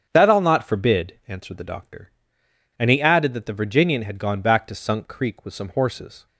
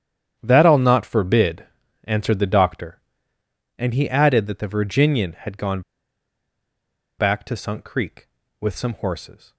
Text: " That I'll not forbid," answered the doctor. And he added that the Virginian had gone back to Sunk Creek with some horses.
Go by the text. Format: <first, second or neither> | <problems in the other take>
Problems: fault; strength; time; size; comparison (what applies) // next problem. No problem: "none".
first | starts louder than the rest; strong; until 1.3 s; 9 dB; strong in the first // pauses between "gone" and "back"; strong; at 5.8 s; 1.3 s long